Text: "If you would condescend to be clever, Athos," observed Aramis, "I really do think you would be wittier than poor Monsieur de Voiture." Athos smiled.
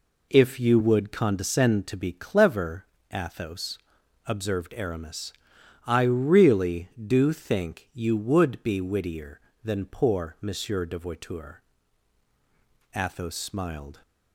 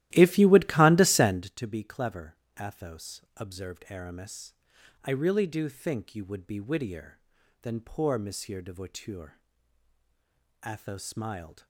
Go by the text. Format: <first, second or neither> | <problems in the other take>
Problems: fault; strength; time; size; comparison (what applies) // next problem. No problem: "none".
first | starts louder than the rest; strong; until 1.5 s; 15 dB